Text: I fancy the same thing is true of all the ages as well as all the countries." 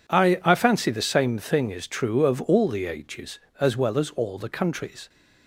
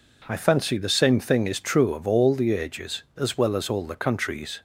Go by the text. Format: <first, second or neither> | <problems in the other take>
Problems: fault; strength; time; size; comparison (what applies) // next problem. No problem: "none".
second | says "I" twice; at 0.4 s